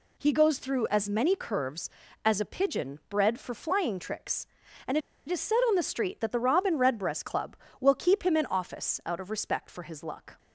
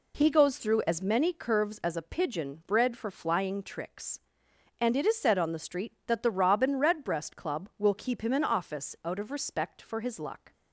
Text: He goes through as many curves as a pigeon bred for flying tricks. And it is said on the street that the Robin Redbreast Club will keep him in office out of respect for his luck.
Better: second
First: pauses between "And" and "it"; slight; at 4.9 s; 0.30 s long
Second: none

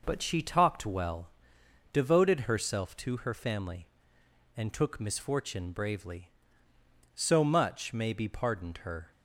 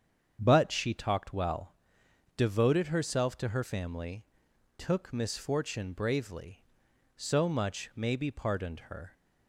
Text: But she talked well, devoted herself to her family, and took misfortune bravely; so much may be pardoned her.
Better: first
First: none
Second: starts louder than the rest; strong; until 1.4 s; 7.5 dB // skips "and"; at 4.4 s

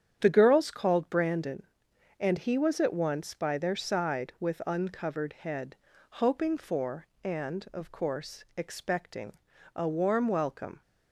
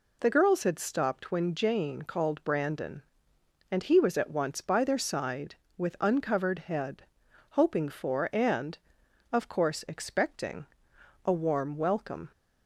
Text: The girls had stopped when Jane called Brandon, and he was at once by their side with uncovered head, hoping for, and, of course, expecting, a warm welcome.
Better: second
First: starts louder than the rest; strong; until 1.2 s; 9 dB // skips "had stopped when Jane"; at 0.6 s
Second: none

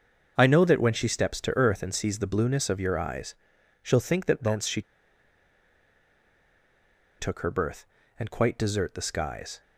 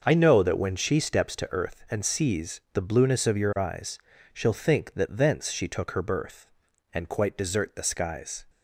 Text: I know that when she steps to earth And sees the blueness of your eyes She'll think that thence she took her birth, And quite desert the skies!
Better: second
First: starts louder than the rest; until 1.3 s; 6.5 dB // pauses between "eyes" and "She'll"; noticeable; at 3.3 s; 0.48 s long // pauses between "she" and "took"; strong; at 4.8 s; 2.3 s long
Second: starts louder than the rest; noticeable; until 1.0 s; 6 dB // pauses between "eyes" and "She'll"; slight; at 3.9 s; 0.36 s long

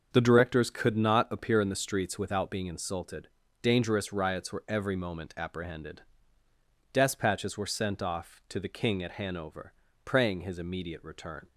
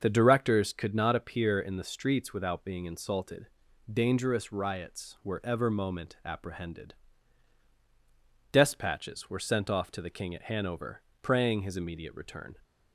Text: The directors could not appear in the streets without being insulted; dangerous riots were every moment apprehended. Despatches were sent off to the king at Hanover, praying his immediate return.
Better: first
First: starts louder than the rest; until 1.1 s; 6.5 dB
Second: starts louder than the rest; until 1.0 s; 6.5 dB // says "ever" for "every"; at 5.4 s

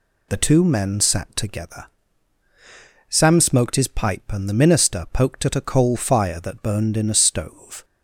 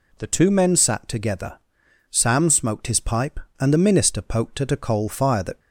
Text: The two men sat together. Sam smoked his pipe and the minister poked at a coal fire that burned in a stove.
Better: first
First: none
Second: stops before "burned in a stove"; at 5.6 s

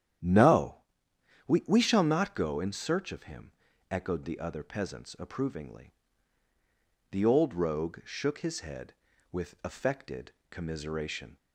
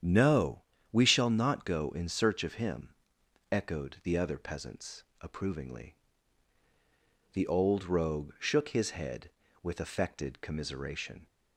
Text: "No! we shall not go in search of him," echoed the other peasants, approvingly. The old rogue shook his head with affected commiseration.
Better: second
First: starts louder than the rest; strong; until 1.9 s; 10 dB // says "we" twice; at 1.6 s // pauses between "affected" and "commiseration"; slight; at 10.3 s; 0.16 s long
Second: starts louder than the rest; strong; until 1.3 s; 9 dB

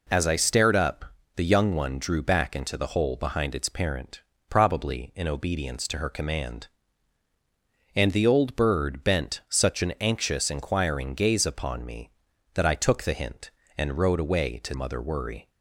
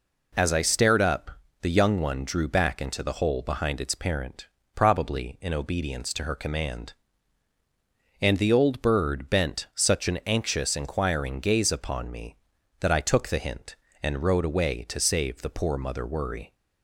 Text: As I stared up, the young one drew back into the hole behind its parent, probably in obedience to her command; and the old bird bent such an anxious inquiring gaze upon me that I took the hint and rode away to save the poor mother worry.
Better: second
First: skips "save the poor"; at 14.7 s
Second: none

